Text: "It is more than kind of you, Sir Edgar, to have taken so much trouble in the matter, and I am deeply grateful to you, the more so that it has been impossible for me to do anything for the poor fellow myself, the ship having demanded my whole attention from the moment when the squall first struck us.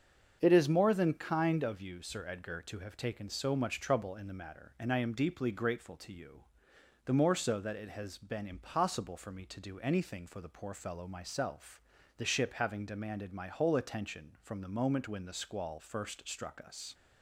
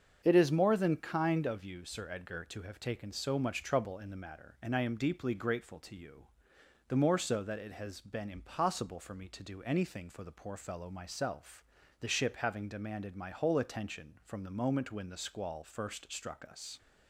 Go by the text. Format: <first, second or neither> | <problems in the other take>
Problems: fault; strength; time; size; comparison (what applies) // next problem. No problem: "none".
neither | starts louder than the rest; the same in both